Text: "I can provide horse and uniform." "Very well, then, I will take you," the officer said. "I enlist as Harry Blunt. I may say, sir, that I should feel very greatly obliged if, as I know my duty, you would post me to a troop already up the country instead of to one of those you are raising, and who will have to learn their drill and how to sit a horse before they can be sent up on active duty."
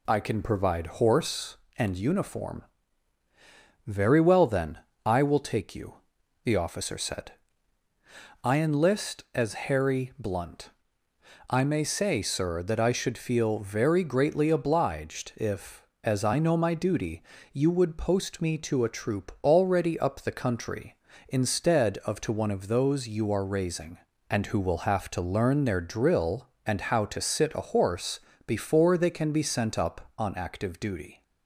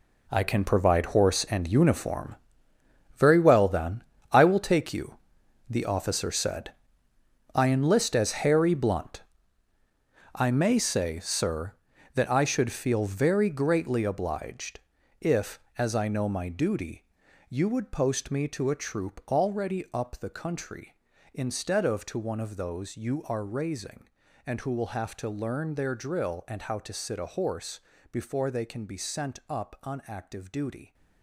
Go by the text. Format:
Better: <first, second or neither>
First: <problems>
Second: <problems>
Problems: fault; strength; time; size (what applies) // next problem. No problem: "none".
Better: first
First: pauses between "horse" and "before"; slight; at 28.2 s; 0.24 s long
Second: gets quieter; strong; throughout; 12 dB // pauses between "obliged" and "if"; at 14.7 s; 0.40 s long // pauses between "horse" and "before"; slight; at 27.7 s; 0.32 s long